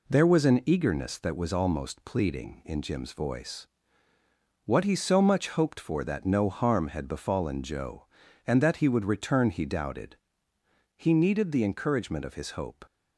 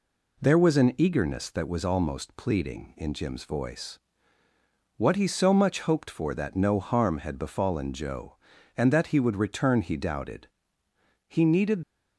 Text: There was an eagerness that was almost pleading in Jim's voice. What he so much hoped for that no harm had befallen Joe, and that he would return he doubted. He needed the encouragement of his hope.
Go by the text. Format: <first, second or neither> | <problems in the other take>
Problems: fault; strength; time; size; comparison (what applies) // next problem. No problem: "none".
first | stops before "the encouragement of his hope"; at 11.8 s